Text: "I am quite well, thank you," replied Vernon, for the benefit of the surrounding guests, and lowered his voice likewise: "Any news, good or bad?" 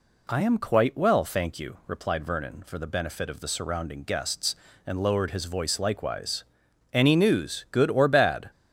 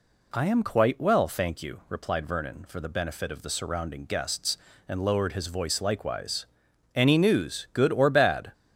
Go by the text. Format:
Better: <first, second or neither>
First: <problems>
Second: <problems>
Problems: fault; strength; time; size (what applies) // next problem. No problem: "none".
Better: neither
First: none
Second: none